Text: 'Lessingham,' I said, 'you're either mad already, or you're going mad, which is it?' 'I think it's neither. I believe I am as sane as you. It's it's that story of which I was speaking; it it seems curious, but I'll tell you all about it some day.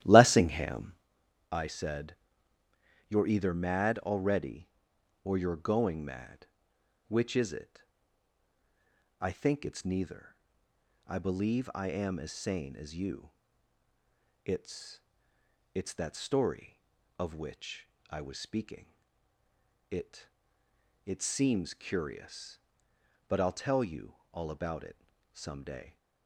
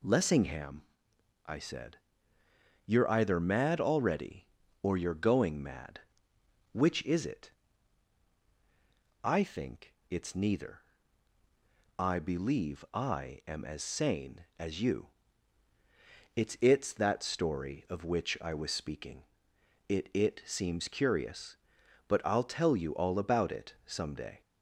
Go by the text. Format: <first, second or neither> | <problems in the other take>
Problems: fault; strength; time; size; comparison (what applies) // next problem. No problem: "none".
second | starts louder than the rest; strong; until 1.1 s; 13.5 dB // pauses between "It's" and "it's"; noticeable; at 15.0 s; 0.74 s long // pauses between "which" and "I"; slight; at 17.8 s; 0.22 s long // pauses between "it" and "it"; noticeable; at 20.2 s; 0.76 s long // pauses between "you" and "all"; slight; at 24.1 s; 0.18 s long // pauses between "it" and "some"; slight; at 24.9 s; 0.34 s long